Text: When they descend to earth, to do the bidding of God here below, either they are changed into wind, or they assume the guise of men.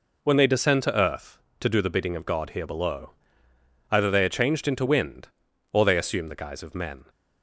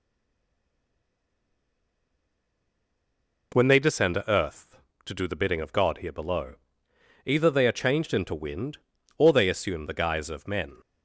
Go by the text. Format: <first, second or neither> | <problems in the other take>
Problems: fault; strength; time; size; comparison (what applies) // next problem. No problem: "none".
first | stays silent before the first word; strong; until 3.5 s; 3.5 s long